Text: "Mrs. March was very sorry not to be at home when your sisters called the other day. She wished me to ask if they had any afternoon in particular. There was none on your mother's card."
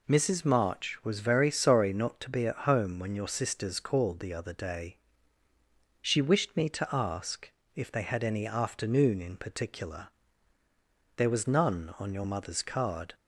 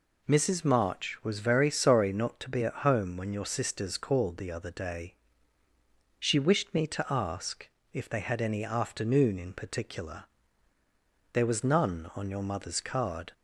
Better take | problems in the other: neither | pauses between "ask" and "if"; slight; the same in both

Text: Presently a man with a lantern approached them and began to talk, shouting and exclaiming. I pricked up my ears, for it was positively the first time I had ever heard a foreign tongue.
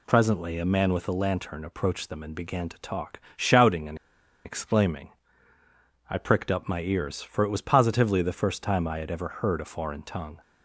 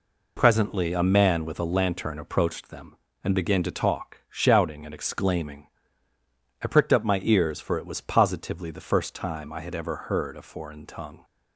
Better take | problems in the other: second | pauses between "and" and "exclaiming"; noticeable; at 3.9 s; 0.48 s long

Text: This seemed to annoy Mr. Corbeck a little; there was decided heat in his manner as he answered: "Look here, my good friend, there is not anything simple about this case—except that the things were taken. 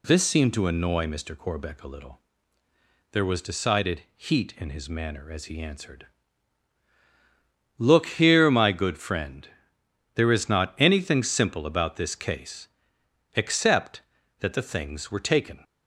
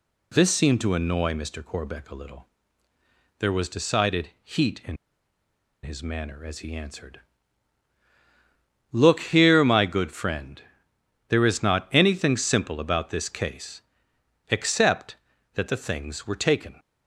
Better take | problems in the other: first | pauses between "in" and "his"; noticeable; at 4.9 s; 0.86 s long

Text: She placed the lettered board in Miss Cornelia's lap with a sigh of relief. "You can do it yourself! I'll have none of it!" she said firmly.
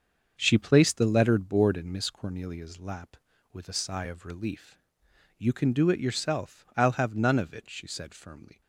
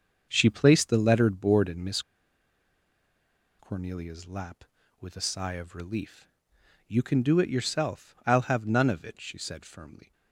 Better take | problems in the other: first | starts louder than the rest; until 1.3 s; 6.5 dB; also in the first // pauses between "Miss" and "Cornelia's"; strong; at 2.0 s; 1.5 s long

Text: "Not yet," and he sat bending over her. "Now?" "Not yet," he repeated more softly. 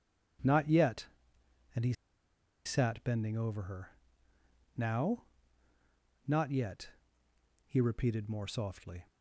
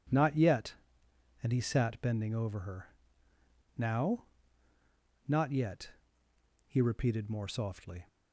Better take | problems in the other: second | pauses between "he" and "sat"; noticeable; at 1.9 s; 0.73 s long

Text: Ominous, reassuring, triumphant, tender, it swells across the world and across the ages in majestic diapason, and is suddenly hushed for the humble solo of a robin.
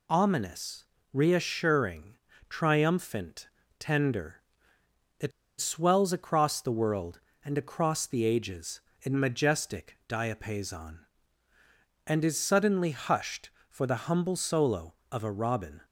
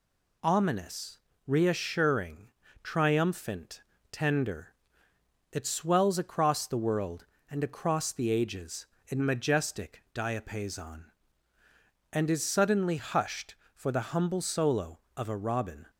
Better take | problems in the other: second | pauses between "it" and "swells"; slight; at 5.3 s; 0.29 s long

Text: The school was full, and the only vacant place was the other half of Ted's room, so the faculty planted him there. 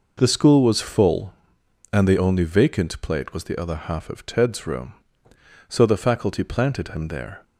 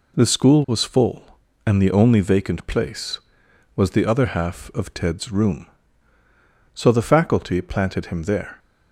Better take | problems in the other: second | says "plate" for "place"; at 3.0 s

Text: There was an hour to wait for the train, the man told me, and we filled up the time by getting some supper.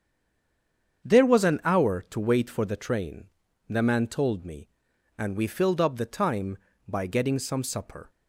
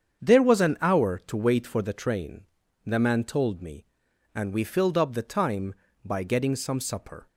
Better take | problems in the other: second | stays silent before the first word; until 1.0 s; 1.0 s long // starts louder than the rest; strong; until 2.1 s; 7.5 dB; strong in the second

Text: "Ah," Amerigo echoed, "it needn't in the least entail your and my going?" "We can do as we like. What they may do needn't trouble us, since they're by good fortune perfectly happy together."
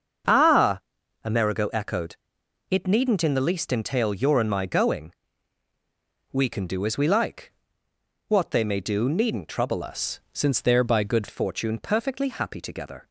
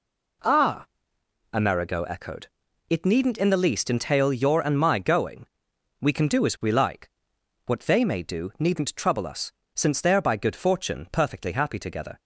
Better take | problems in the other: second | starts louder than the rest; until 1.7 s; 6.5 dB // changes voice from "us" to "good"; from 9.8 to 11.2 s; 1.4 s long

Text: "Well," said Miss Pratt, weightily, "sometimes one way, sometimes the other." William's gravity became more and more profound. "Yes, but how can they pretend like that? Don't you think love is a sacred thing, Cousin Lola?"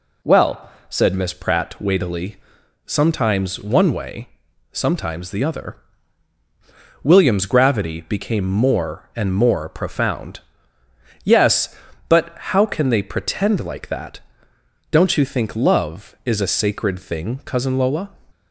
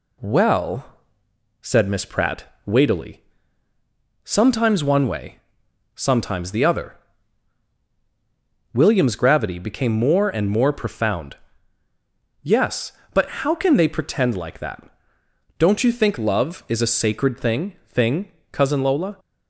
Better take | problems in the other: first | says "thing" twice; at 17.8 s

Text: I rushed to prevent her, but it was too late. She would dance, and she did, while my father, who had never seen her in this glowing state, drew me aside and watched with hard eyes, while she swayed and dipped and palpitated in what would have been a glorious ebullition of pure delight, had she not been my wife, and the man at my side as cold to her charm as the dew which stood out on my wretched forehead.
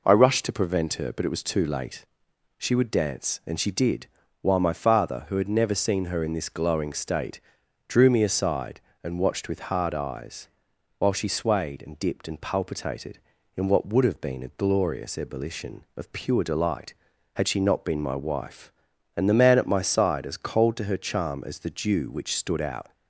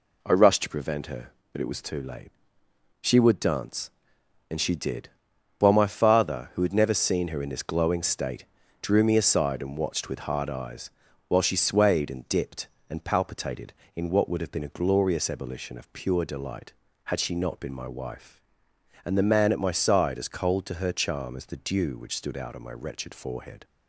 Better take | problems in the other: second | stops before "on my wretched forehead"; at 22.9 s

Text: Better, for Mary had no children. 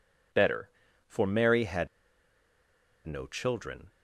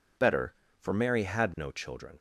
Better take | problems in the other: second | pauses between "had" and "no"; at 1.8 s; 1.1 s long

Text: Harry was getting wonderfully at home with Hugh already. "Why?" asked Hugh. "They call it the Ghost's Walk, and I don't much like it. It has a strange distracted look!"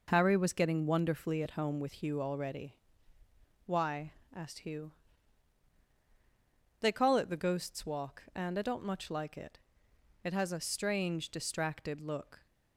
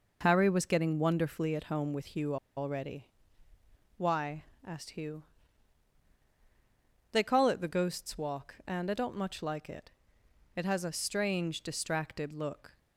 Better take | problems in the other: first | pauses between "Hugh" and "already"; slight; at 2.3 s; 0.21 s long

